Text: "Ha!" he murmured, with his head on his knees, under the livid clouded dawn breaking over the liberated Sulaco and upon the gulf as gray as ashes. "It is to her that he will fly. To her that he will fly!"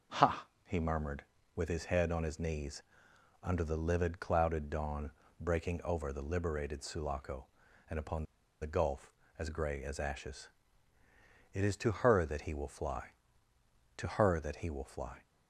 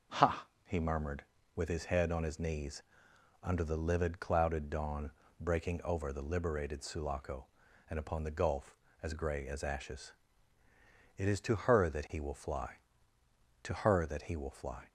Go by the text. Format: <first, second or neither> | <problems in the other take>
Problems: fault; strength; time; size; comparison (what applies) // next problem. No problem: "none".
second | pauses between "dawn" and "breaking"; slight; at 5.1 s; 0.28 s long; slight in the second // pauses between "upon" and "the"; at 8.2 s; 0.37 s long